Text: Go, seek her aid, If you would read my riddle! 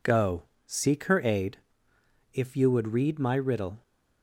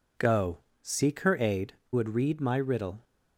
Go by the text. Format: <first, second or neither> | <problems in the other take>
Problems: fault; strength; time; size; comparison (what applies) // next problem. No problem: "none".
first | skips "If you"; at 1.8 s